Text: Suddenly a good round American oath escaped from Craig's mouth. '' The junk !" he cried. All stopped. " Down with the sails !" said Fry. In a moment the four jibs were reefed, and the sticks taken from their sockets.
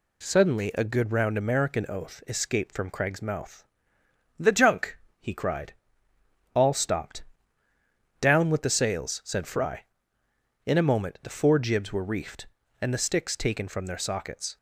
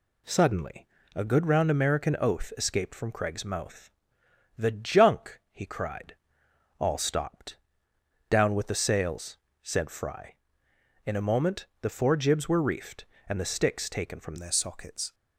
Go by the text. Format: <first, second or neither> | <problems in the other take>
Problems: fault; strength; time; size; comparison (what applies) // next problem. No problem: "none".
first | pauses between "Suddenly" and "a"; slight; at 0.8 s; 0.28 s long // pauses between "moment" and "the"; slight; at 11.6 s; 0.16 s long // changes voice at "their"; from 14.3 s on; 0.8 s long